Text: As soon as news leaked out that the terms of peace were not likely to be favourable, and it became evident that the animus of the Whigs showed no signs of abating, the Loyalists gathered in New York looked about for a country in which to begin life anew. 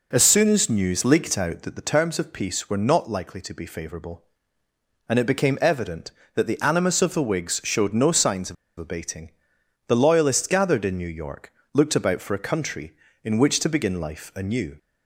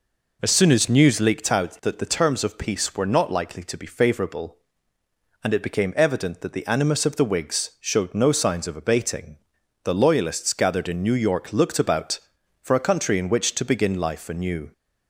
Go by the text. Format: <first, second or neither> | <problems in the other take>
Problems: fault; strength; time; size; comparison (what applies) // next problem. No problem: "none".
second | pauses between "of" and "abating"; slight; at 8.5 s; 0.24 s long // pauses between "York" and "looked"; slight; at 11.5 s; 0.20 s long